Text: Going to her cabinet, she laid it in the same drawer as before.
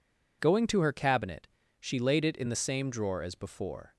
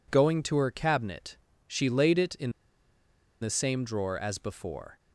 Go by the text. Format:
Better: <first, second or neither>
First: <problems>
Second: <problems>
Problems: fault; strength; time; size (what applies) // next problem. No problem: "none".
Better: first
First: none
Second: pauses between "in" and "the"; noticeable; at 2.4 s; 0.92 s long